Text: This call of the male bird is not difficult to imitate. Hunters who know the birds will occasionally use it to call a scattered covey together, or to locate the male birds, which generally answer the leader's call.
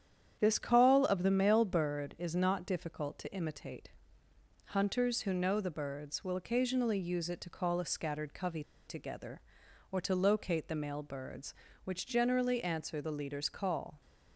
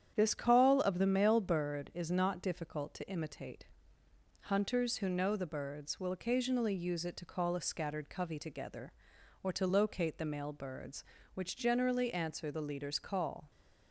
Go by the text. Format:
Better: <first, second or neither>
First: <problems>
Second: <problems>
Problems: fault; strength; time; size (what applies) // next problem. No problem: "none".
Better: second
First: starts louder than the rest; strong; until 1.4 s; 9 dB // pauses between "covey" and "together"; slight; at 8.6 s; 0.25 s long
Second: starts louder than the rest; strong; until 1.1 s; 9 dB